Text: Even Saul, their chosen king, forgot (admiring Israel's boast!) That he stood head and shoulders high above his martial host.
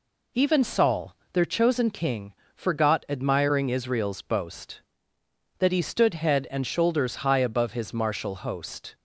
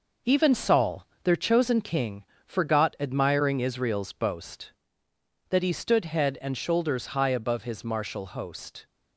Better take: first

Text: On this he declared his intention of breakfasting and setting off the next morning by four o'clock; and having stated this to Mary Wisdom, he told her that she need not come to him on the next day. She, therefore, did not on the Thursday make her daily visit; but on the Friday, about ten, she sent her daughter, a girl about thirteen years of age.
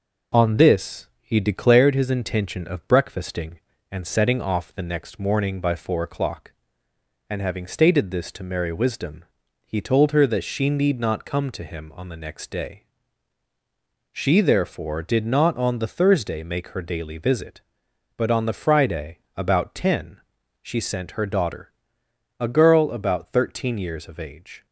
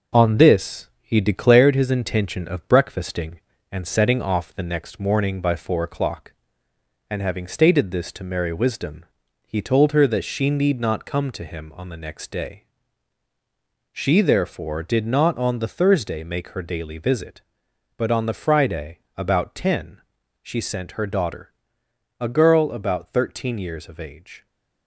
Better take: first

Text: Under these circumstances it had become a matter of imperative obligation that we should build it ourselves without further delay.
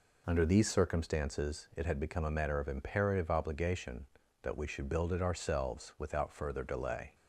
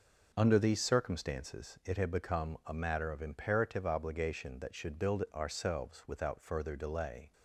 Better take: first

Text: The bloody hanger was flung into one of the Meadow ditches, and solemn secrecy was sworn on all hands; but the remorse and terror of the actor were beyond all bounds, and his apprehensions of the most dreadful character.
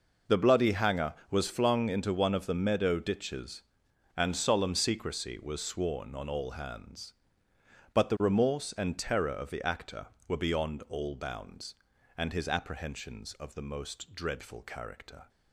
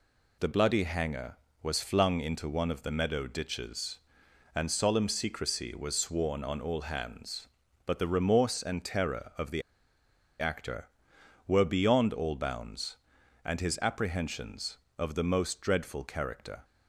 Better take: first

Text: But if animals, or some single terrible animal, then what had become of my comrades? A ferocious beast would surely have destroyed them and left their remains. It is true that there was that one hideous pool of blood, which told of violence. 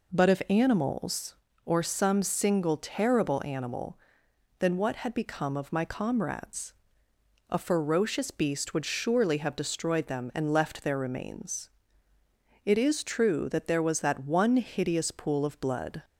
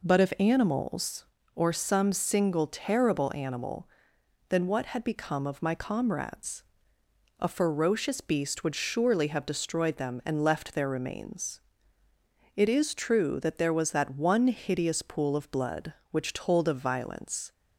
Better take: second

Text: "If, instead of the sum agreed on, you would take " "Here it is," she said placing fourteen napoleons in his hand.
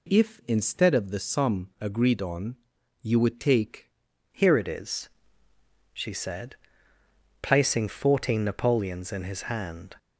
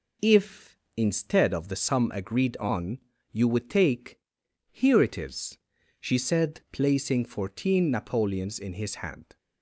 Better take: second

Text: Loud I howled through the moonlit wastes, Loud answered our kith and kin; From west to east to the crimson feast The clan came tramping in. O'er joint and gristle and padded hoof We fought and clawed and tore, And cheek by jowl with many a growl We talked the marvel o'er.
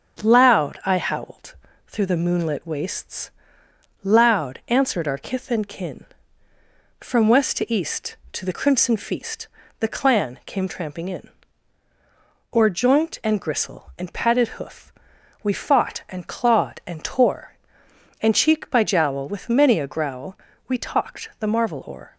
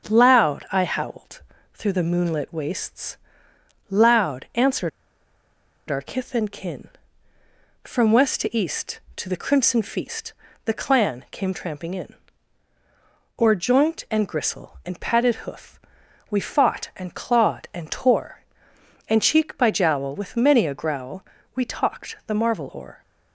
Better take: first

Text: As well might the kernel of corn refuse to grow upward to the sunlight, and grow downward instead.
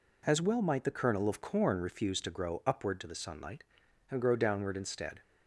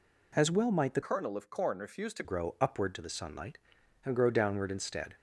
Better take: first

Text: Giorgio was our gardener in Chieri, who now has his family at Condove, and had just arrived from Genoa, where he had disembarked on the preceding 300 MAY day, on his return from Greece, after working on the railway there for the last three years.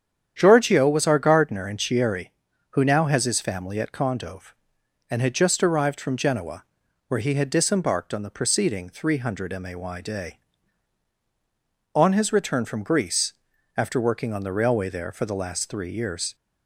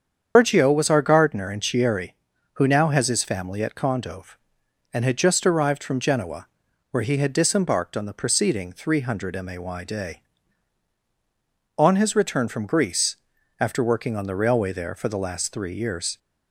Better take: first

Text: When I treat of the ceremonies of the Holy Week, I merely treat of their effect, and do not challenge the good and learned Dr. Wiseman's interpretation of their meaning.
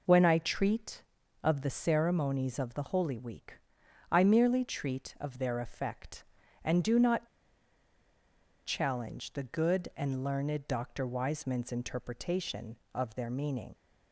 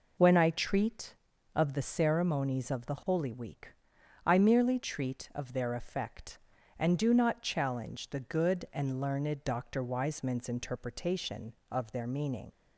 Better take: second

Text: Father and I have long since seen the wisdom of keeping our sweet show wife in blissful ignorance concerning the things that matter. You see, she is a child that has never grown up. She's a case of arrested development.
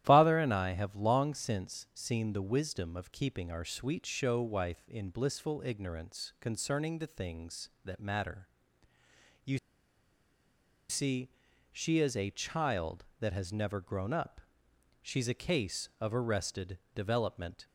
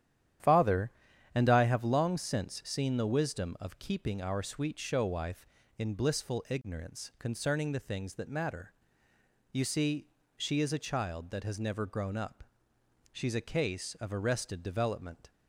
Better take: second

